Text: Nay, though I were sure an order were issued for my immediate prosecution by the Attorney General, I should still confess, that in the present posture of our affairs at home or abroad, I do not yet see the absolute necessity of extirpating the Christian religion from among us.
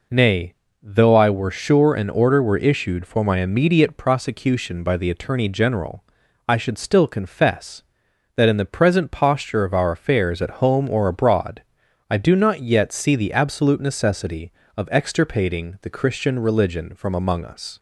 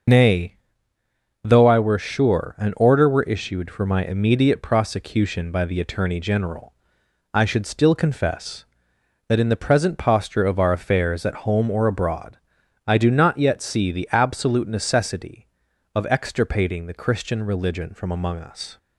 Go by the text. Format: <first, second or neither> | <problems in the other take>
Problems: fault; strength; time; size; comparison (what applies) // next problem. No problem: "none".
first | loses the start of "Nay"; at 0.0 s; 70 ms // starts louder than the rest; until 1.9 s; 6 dB